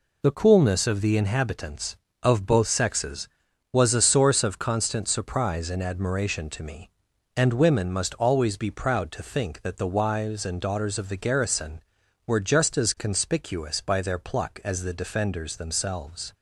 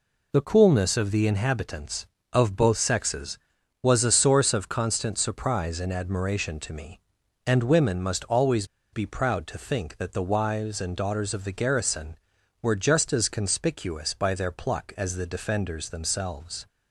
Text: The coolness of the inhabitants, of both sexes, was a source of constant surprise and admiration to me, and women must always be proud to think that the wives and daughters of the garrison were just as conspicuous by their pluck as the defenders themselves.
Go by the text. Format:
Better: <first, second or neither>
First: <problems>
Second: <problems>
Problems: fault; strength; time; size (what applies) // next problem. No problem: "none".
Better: first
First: none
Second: pauses between "always" and "be"; slight; at 8.6 s; 0.27 s long